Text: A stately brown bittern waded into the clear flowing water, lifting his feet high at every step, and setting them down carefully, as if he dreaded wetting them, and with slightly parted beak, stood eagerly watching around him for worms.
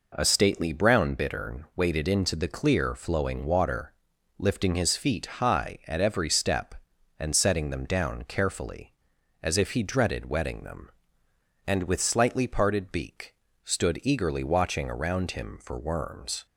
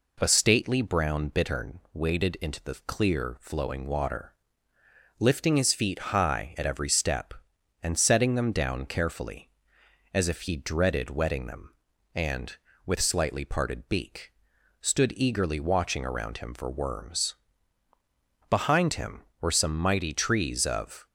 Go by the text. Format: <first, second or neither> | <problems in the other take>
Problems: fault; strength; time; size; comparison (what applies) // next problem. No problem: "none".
first | goes on to say "Behind him were some mighty trees of"; strong; from 18.4 s on; 2.5 s long